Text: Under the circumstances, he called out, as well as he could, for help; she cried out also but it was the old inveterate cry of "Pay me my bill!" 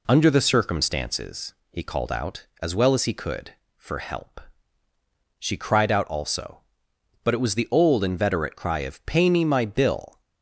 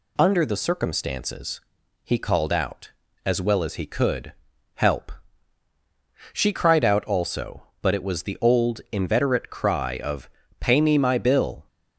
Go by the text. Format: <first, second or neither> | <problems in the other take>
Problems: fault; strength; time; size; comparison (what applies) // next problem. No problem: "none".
first | skips "for"; at 4.5 s // pauses between "of" and "Pay"; slight; at 10.2 s; 0.32 s long